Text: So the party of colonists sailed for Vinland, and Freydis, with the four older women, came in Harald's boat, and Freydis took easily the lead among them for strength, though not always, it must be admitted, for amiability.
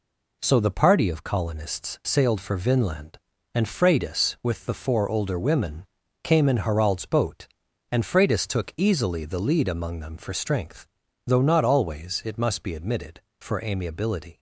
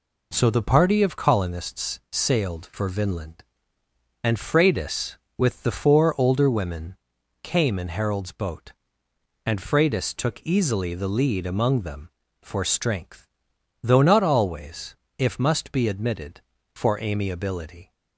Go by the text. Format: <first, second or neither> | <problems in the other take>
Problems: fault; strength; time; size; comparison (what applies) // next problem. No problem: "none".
first | says "if" for "it"; at 15.1 s